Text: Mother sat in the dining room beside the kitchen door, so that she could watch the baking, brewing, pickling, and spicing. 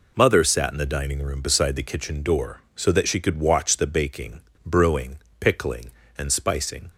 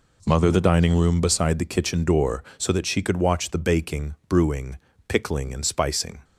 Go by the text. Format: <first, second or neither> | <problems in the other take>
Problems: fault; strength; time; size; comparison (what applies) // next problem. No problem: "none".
first | skips "sat in"; at 0.5 s